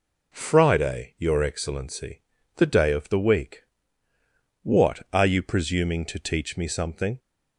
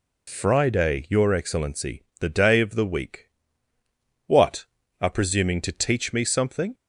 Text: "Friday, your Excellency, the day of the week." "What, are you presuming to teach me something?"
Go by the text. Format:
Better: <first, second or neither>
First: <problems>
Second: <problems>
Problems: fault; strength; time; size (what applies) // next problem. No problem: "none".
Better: first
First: none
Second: skips "you"; at 5.0 s